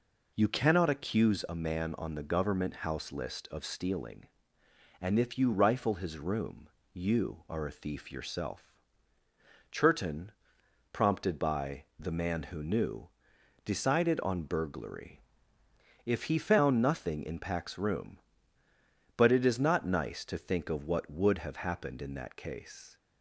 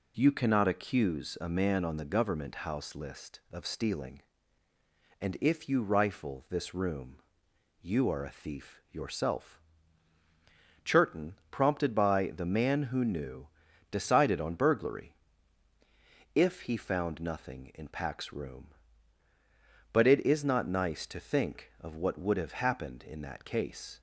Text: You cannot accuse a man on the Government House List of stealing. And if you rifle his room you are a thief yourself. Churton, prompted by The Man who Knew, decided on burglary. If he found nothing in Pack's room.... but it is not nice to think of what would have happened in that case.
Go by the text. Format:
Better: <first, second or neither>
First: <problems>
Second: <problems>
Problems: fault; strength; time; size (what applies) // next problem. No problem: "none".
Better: first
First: pauses between "room" and "you"; slight; at 6.6 s; 0.26 s long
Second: says "this" for "his"; at 6.4 s // pauses between "room" and "you"; noticeable; at 7.1 s; 0.64 s long